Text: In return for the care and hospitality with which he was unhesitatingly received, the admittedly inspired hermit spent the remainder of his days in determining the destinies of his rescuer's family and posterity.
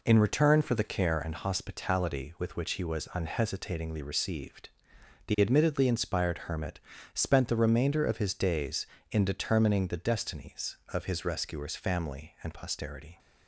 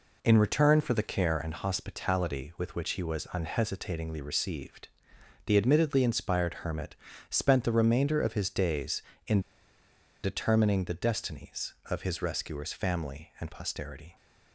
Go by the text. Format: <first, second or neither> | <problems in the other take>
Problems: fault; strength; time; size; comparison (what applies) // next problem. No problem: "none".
first | pauses between "hermit" and "spent"; slight; at 6.9 s; 0.36 s long; slight in the first // pauses between "in" and "determining"; noticeable; at 9.3 s; 0.83 s long